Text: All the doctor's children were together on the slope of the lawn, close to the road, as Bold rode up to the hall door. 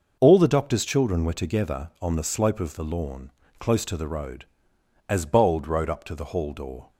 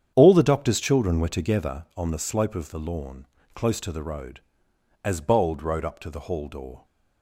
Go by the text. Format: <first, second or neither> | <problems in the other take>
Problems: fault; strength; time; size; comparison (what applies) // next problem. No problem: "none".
first | starts louder than the rest; strong; until 1.8 s; 8.5 dB